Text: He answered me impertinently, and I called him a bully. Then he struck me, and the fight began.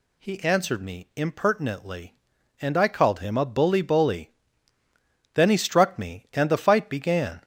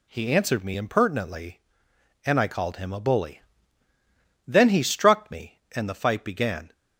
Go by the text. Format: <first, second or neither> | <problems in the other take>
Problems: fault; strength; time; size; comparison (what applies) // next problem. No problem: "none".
second | says "bully" twice; at 3.7 s